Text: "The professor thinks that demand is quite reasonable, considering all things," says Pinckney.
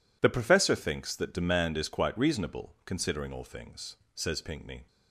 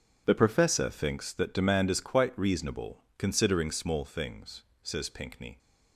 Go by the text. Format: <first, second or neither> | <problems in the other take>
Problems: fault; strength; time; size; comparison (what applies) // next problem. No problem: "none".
first | starts louder than the rest; until 1.2 s; 6.5 dB // says "small" for "all"; at 3.7 s